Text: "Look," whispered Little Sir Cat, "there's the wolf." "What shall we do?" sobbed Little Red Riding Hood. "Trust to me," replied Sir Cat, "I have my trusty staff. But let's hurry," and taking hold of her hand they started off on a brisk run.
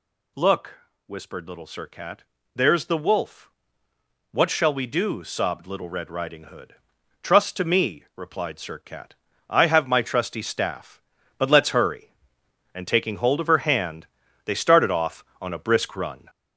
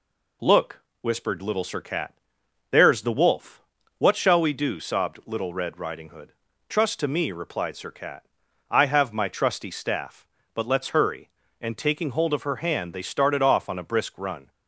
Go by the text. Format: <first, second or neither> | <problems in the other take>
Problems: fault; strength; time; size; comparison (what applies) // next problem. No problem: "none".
second | gets louder; noticeable; throughout; 5 dB // pauses between "hand" and "they"; slight; at 14.0 s; 0.36 s long